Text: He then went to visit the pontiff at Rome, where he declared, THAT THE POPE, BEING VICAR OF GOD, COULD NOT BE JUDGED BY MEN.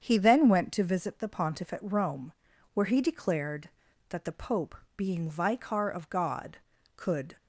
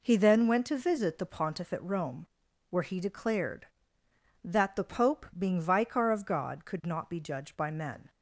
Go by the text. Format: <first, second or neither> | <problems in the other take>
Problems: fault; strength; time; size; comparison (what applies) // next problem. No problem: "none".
second | starts louder than the rest; strong; until 1.0 s; 7.5 dB // stops before "NOT BE JUDGED BY MEN"; at 7.3 s